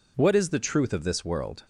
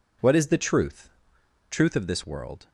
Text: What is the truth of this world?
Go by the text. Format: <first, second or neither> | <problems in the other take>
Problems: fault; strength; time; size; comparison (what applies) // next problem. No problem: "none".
first | says "truth" twice; at 1.7 s